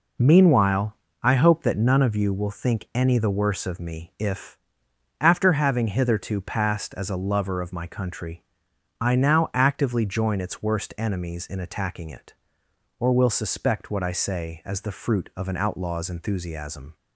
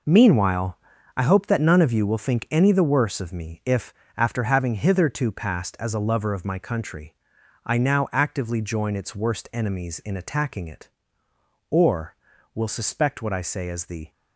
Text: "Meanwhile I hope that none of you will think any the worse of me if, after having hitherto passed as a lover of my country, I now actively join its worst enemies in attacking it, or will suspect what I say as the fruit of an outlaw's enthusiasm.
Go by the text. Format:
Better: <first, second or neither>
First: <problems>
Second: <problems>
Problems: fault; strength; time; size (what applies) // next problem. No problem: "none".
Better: first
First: pauses between "Meanwhile" and "I"; slight; at 0.9 s; 0.30 s long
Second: pauses between "Meanwhile" and "I"; at 0.7 s; 0.38 s long // stops before "fruit of an outlaw's enthusiasm"; at 14.0 s